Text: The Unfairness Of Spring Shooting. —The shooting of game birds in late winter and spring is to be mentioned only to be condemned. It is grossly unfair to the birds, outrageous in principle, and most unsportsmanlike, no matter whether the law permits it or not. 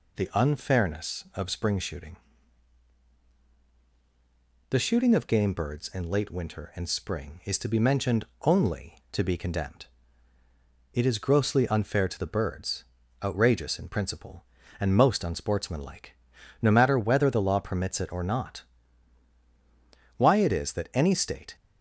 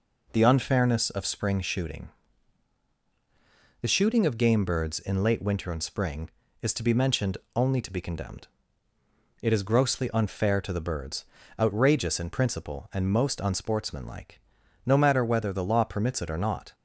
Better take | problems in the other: second | pauses between "mentioned" and "only"; slight; at 8.2 s; 0.16 s long; slight in the second // goes on to say "Why it is that any state"; from 20.1 s on; 1.3 s long

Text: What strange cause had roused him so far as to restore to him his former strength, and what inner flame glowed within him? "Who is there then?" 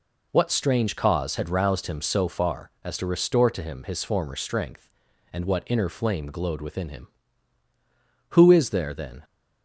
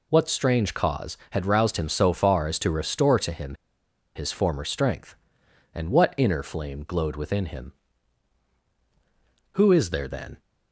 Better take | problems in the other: first | pauses between "him" and "his"; noticeable; at 3.5 s; 0.61 s long

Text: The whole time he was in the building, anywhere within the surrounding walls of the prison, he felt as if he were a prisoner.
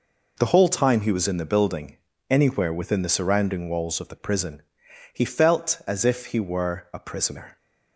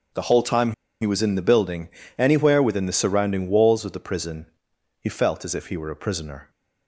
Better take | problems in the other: first | pauses between "time" and "he"; slight; at 0.7 s; 0.28 s long

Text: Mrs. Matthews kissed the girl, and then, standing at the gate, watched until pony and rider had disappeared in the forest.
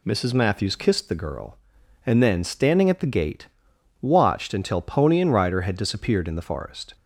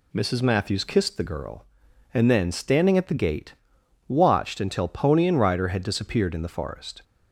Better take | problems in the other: neither | none

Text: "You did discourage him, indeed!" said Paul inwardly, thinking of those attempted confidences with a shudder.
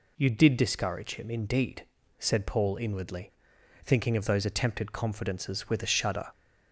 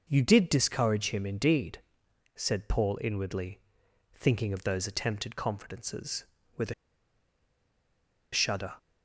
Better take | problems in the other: first | pauses between "a" and "shudder"; strong; at 6.7 s; 1.5 s long

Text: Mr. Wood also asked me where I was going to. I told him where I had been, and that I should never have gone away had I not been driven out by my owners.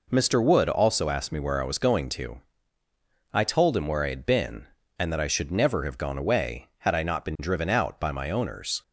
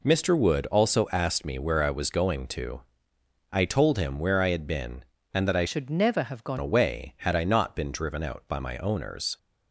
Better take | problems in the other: first | changes voice from "should" to "gone"; from 5.6 to 6.5 s; 0.9 s long

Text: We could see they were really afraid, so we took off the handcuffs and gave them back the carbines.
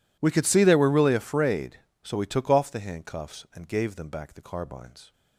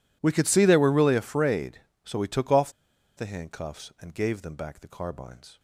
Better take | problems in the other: first | pauses between "off" and "the"; at 2.7 s; 0.45 s long

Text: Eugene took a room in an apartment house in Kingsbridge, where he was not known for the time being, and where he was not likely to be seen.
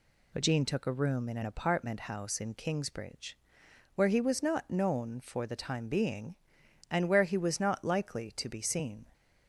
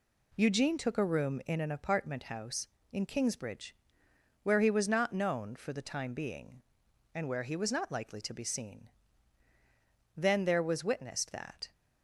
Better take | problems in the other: first | goes on to say "Then there was witnessed that"; from 10.1 s on; 1.5 s long

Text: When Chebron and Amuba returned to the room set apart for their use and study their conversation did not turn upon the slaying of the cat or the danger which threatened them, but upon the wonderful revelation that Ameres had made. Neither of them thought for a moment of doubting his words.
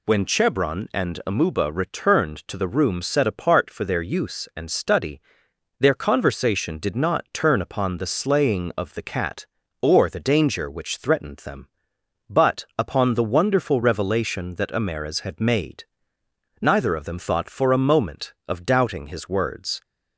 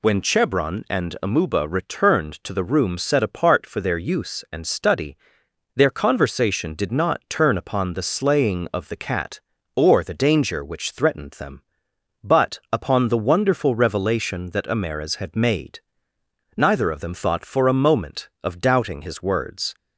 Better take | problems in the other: neither | pauses between "study" and "their"; noticeable; the same in both

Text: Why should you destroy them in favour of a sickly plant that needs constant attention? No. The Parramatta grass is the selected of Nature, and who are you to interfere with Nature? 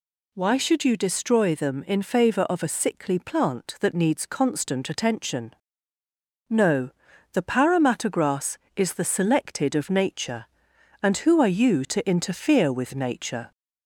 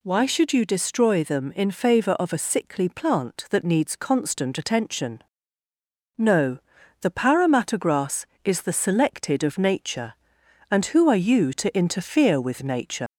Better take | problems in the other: first | leaves "Nature" unfinished; at 13.0 s; 130 ms

